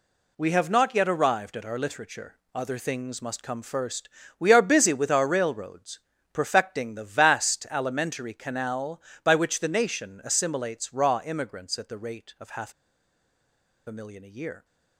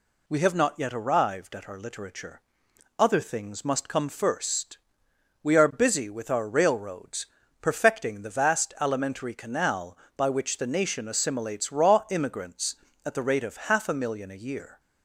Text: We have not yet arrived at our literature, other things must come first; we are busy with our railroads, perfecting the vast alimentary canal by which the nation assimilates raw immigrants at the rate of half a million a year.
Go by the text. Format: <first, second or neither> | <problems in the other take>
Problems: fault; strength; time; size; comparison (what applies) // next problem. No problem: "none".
second | pauses between "half" and "a"; at 12.7 s; 1.1 s long